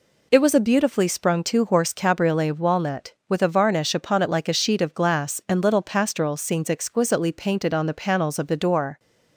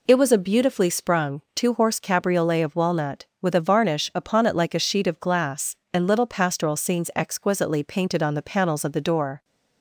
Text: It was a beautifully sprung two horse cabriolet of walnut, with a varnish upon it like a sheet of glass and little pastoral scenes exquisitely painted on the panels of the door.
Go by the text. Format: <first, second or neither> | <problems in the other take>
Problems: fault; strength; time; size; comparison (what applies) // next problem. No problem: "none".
neither | none